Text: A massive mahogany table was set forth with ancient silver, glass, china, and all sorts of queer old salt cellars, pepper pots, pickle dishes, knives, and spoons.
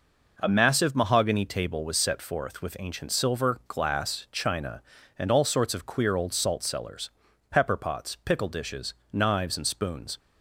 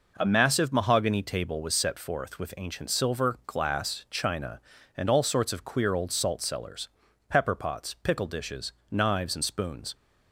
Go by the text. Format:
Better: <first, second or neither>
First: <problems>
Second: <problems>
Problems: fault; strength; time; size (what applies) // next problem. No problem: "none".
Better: neither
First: none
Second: none